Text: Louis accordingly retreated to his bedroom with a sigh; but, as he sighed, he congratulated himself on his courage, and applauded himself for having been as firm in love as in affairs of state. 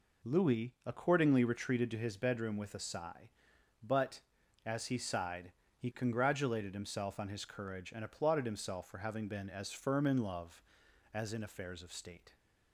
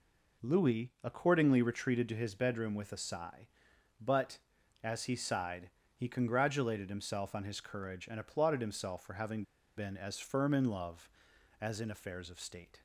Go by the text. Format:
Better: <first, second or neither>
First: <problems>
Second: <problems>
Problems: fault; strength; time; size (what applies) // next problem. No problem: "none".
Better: first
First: none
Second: pauses between "having" and "been"; slight; at 9.4 s; 0.33 s long